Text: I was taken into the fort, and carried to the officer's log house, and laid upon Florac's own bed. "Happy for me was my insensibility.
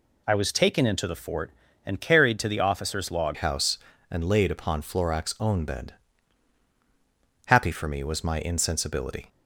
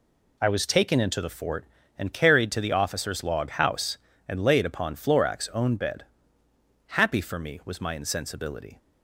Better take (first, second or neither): second